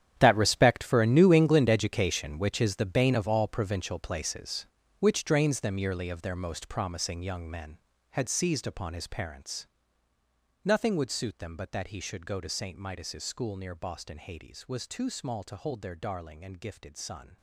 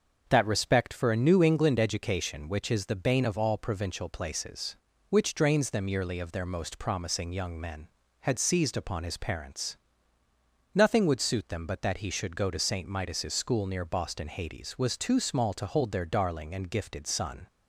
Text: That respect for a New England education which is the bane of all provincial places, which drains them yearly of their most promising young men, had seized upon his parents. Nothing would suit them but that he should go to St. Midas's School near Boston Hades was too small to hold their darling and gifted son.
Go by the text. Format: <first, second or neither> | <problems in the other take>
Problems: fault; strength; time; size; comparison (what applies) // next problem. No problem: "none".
second | gets quieter; strong; throughout; 15 dB // starts louder than the rest; strong; until 1.1 s; 10 dB; also in the second